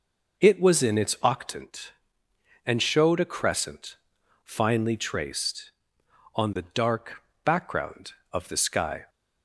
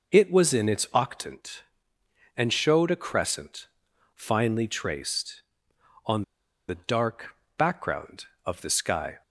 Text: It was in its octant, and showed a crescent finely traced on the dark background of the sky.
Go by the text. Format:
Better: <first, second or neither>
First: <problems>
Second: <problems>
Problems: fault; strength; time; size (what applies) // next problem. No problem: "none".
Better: first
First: pauses between "crescent" and "finely"; noticeable; at 3.9 s; 0.48 s long // pauses between "dark" and "background"; slight; at 7.2 s; 0.22 s long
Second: pauses between "crescent" and "finely"; noticeable; at 3.6 s; 0.48 s long // pauses between "on" and "the"; noticeable; at 6.2 s; 0.46 s long // pauses between "dark" and "background"; slight; at 7.3 s; 0.22 s long